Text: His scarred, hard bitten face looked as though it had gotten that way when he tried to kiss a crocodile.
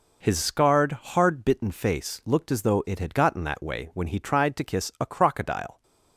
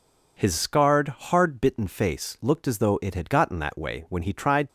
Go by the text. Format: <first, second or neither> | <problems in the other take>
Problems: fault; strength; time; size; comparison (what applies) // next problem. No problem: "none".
first | stops before "to kiss a crocodile"; at 4.6 s